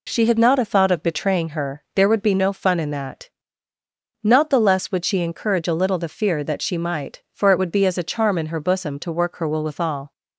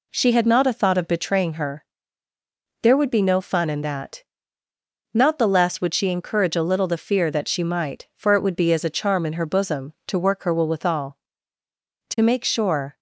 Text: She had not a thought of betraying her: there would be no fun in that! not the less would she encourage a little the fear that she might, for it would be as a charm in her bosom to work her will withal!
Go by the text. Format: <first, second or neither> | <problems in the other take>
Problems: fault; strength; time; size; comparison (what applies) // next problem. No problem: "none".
first | goes on to say "To make sure"; noticeable; from 12.0 s on; 0.90 s long